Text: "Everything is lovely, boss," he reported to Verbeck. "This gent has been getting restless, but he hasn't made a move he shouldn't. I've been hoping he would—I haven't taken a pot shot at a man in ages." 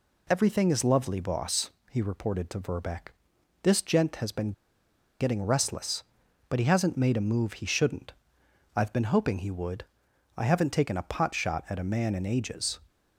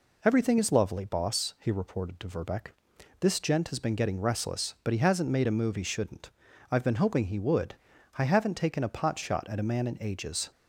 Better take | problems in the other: second | pauses between "been" and "getting"; noticeable; at 4.5 s; 0.68 s long

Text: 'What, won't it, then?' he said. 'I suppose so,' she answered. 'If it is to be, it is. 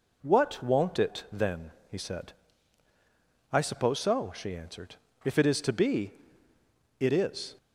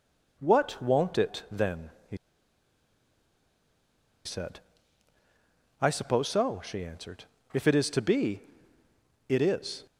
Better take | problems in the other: first | pauses between "he" and "said"; strong; at 2.1 s; 2.0 s long

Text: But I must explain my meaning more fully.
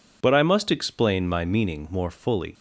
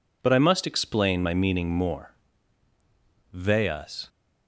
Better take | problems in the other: first | says "veas" for "fully"; at 3.3 s

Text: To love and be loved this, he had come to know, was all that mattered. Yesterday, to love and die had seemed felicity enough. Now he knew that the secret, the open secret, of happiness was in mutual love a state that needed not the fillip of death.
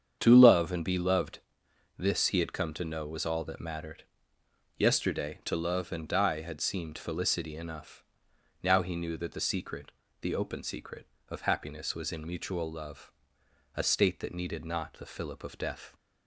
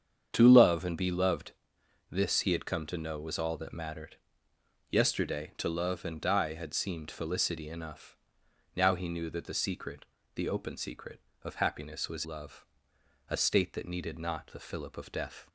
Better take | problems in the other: first | starts louder than the rest; strong; until 1.3 s; 7.5 dB; strong in the first // pauses between "loved" and "this"; noticeable; at 1.5 s; 0.58 s long; noticeable in the first // skips "in mutual"; at 12.2 s // pauses between "love" and "a"; noticeable; at 12.6 s; 0.66 s long; noticeable in the first

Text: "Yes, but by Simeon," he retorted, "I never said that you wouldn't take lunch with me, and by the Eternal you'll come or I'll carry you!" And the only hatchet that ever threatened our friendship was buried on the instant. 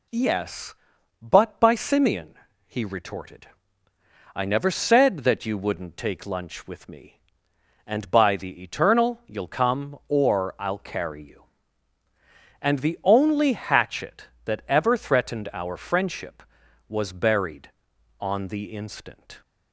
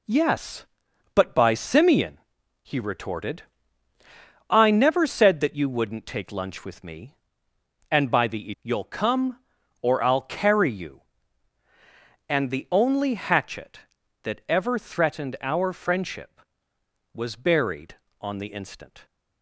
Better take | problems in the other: first | skips "Eternal"; at 8.5 s

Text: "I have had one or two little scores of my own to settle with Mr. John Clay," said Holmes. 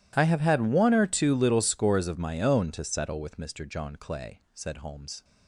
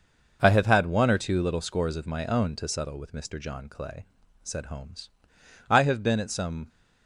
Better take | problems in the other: first | goes on to say "I have been at some"; noticeable; from 5.6 s on; 1.0 s long

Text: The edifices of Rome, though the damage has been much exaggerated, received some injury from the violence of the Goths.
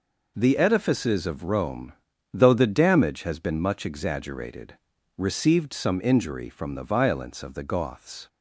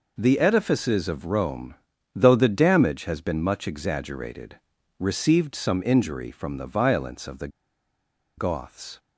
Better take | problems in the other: first | pauses between "the" and "Goths"; noticeable; at 7.4 s; 0.89 s long

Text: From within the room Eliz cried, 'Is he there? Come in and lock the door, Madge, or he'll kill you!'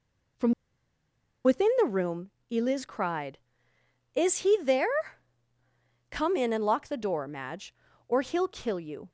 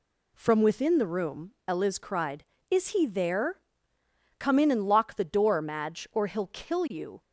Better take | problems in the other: second | pauses between "From" and "within"; noticeable; at 0.5 s; 0.93 s long // pauses between "room" and "Eliz"; slight; at 2.3 s; 0.20 s long

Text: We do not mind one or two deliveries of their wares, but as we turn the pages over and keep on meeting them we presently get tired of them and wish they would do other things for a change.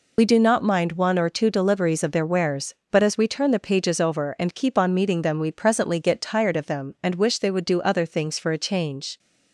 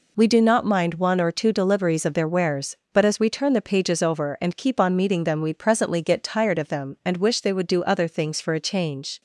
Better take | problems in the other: second | loses the start of "We"; at 0.1 s; 40 ms

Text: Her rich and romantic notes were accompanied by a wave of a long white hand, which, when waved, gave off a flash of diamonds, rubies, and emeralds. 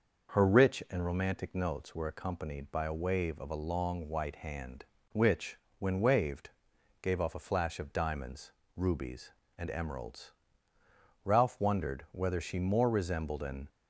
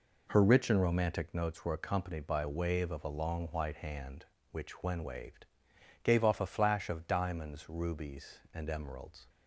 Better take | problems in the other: second | goes on to say "Ralph wondered whether she more resembled an"; strong; from 11.2 s on; 2.4 s long

